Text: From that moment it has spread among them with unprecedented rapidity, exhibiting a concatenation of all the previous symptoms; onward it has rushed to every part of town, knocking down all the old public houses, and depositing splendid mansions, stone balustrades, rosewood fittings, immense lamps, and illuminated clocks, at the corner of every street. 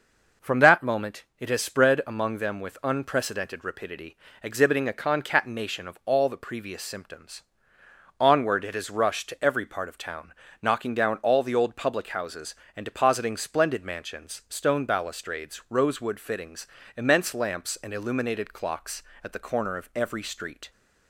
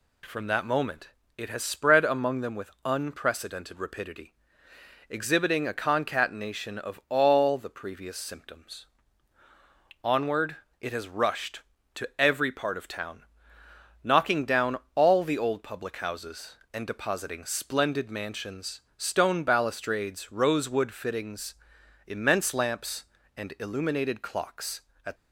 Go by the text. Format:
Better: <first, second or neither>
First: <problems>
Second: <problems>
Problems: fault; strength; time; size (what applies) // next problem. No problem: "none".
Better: first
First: none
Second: pauses between "moment" and "it"; slight; at 1.1 s; 0.26 s long // pauses between "onward" and "it"; slight; at 10.5 s; 0.24 s long // pauses between "down" and "all"; slight; at 14.7 s; 0.16 s long // stops before "the corner of every street"; at 25.1 s